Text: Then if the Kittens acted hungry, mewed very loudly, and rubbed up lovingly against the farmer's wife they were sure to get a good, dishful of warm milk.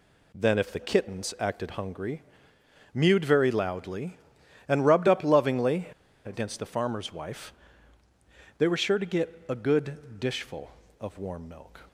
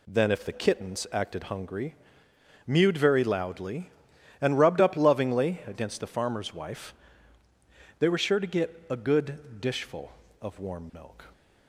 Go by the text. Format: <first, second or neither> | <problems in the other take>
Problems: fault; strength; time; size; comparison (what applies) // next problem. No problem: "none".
second | pauses between "lovingly" and "against"; at 5.8 s; 0.37 s long // pauses between "wife" and "they"; at 7.5 s; 1.0 s long; also in the second